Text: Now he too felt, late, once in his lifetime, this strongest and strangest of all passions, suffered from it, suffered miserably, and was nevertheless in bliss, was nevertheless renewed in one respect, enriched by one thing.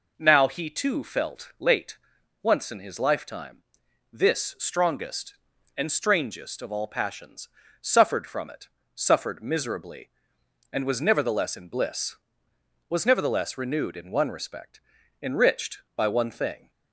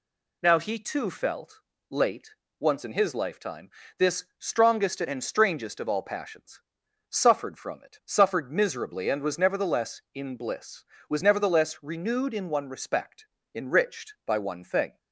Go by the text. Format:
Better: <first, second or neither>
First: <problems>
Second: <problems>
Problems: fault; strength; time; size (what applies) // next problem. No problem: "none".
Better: neither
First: none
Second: none